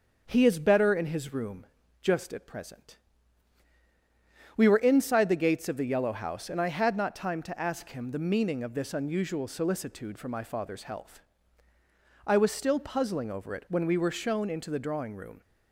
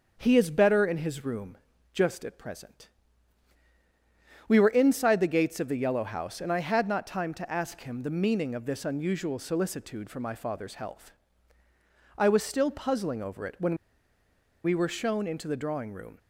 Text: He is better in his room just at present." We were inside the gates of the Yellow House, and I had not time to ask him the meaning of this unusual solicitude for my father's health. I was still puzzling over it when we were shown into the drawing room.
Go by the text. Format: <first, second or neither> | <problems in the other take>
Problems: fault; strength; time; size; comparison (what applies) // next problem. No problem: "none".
first | starts louder than the rest; until 1.1 s; 6.5 dB; also in the first // pauses between "room" and "just"; slight; at 1.5 s; 0.36 s long; slight in the first // pauses between "when" and "we"; noticeable; at 13.7 s; 0.89 s long